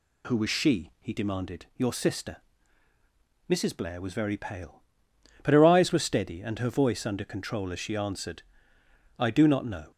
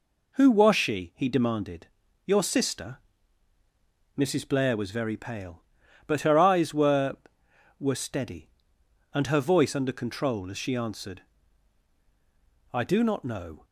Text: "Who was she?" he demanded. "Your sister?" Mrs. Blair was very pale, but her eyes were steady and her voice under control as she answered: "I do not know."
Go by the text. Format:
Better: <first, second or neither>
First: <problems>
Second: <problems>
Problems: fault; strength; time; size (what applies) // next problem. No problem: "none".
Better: first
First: none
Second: says "were" twice; at 7.8 s